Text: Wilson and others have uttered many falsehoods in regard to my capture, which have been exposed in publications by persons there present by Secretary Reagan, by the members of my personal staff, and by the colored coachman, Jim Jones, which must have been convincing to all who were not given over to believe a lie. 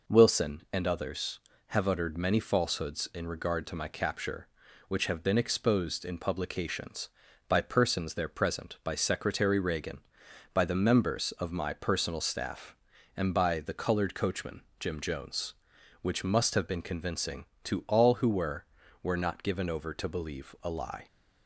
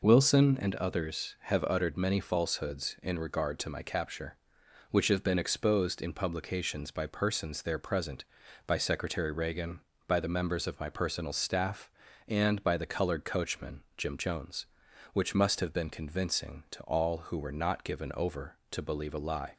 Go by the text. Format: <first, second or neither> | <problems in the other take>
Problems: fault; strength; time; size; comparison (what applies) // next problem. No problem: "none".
second | says "were" twice; at 19.0 s